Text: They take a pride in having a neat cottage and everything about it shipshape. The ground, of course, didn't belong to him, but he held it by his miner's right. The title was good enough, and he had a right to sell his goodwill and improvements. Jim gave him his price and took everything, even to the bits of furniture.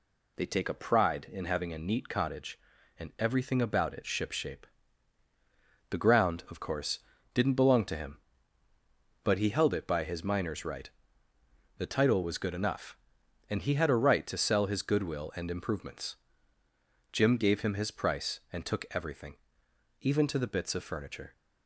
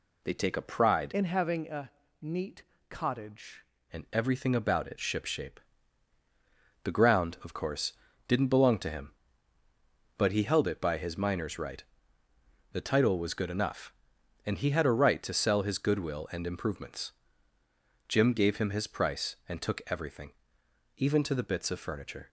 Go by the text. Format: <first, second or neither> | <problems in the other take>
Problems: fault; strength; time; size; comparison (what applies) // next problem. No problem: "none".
first | changes voice from "in" to "cottage"; from 1.1 to 3.6 s; 2.5 s long // pauses between "a" and "neat"; slight; at 1.9 s; 0.30 s long // pauses between "neat" and "cottage"; slight; at 2.6 s; 0.26 s long